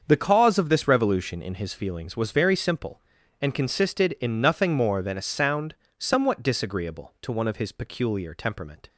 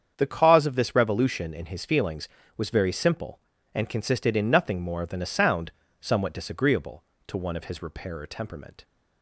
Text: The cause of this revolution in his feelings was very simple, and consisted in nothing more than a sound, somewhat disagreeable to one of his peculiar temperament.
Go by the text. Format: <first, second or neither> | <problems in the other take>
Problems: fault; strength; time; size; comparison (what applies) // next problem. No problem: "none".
first | starts louder than the rest; strong; until 1.1 s; 8 dB; also in the first // says "repairer" for "peculiar"; at 7.8 s